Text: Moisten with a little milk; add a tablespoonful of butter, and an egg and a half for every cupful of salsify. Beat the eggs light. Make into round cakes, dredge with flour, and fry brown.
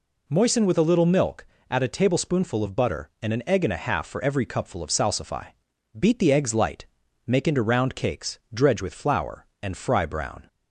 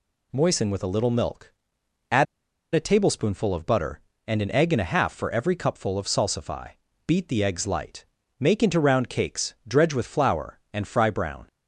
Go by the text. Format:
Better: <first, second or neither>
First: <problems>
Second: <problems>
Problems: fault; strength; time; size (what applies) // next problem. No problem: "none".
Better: first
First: none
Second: pauses between "add" and "a"; noticeable; at 2.2 s; 0.49 s long